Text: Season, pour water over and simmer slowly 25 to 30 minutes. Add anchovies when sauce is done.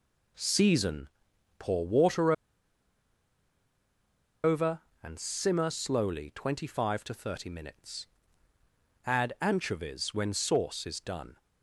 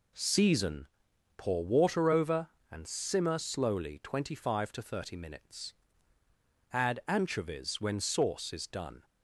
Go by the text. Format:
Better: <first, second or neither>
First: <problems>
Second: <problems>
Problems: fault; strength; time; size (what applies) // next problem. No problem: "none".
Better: second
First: pauses between "water" and "over"; strong; at 2.3 s; 2.1 s long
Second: none